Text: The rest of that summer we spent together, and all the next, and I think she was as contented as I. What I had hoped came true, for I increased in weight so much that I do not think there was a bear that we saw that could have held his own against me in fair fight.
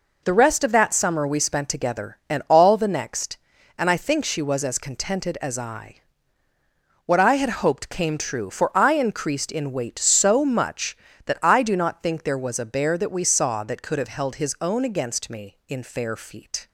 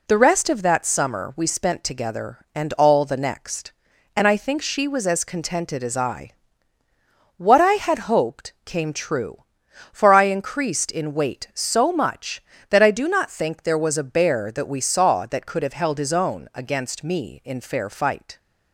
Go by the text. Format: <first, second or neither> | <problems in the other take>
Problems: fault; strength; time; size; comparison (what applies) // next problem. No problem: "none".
second | says "feet" for "fight"; at 16.1 s